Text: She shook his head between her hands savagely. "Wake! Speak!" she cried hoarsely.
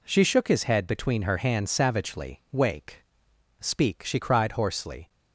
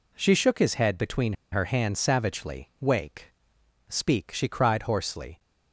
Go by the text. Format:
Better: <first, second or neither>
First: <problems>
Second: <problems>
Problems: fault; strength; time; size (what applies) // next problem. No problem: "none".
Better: first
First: none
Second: pauses between "between" and "her"; slight; at 1.3 s; 0.19 s long